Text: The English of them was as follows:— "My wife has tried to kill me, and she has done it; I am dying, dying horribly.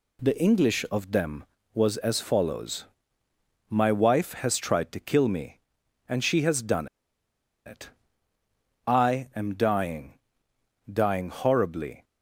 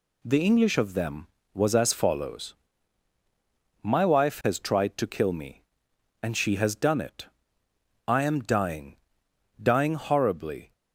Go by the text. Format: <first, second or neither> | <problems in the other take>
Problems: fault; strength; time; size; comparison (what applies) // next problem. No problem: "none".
second | pauses between "done" and "it"; noticeable; at 6.8 s; 0.79 s long